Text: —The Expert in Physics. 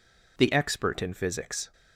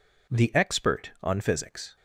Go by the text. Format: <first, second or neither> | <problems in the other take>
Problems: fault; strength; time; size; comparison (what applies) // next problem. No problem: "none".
first | says "on" for "in"; at 1.2 s